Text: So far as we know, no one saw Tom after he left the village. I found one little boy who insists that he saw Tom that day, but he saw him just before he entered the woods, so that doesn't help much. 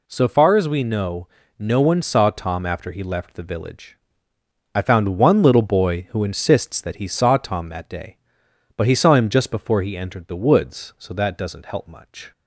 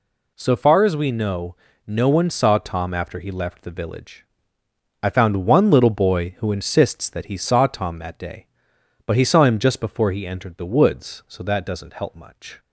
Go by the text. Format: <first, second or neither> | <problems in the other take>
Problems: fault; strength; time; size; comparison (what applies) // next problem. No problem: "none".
neither | none